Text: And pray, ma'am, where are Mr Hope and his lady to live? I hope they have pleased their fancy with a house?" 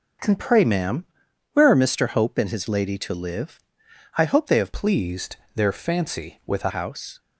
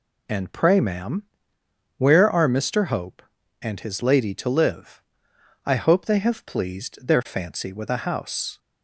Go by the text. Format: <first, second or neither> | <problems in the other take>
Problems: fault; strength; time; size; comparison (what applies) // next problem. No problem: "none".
second | starts louder than the rest; until 1.7 s; 6 dB // changes voice from "pleased" to "a"; from 4.7 to 6.7 s; 2.0 s long // pauses between "pleased" and "their"; slight; at 5.3 s; 0.18 s long